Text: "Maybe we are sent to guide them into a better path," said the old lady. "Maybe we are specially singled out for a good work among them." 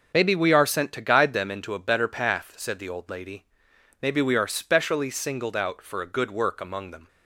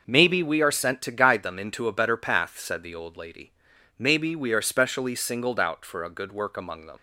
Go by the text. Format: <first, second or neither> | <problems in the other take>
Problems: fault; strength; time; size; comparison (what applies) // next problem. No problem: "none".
first | starts louder than the rest; noticeable; until 1.0 s; 6 dB; also in the first // leaves "them" unfinished; at 6.9 s; 80 ms